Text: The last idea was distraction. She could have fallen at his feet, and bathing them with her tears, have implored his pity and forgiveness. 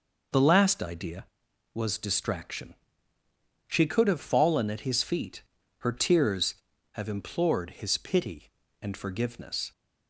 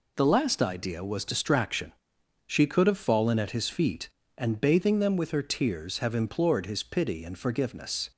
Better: second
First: skips "and bathing them with"; at 5.6 s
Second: none

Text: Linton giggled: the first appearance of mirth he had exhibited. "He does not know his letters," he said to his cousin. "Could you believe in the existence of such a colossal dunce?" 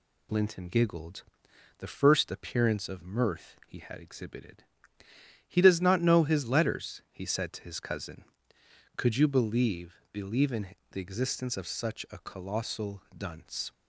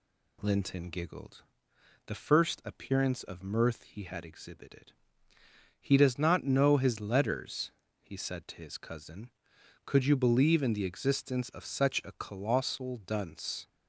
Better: second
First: says "believe" twice; at 10.1 s // pauses between "in" and "the"; slight; at 10.7 s; 0.16 s long // pauses between "colossal" and "dunce"; slight; at 13.0 s; 0.16 s long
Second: none

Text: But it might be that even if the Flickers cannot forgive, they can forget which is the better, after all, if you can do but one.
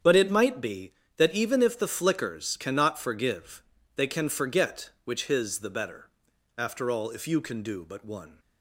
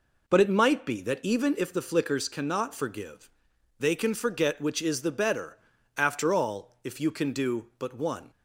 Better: second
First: starts louder than the rest; strong; until 1.2 s; 8.5 dB // says "his" for "is"; at 5.2 s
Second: none

